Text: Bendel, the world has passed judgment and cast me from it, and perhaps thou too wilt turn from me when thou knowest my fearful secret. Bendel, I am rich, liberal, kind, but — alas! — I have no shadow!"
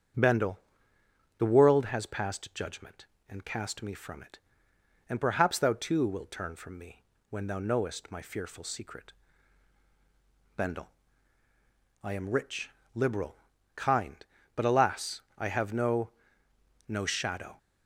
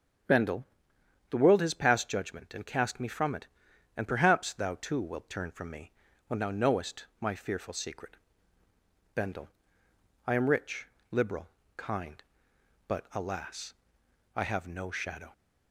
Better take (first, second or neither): second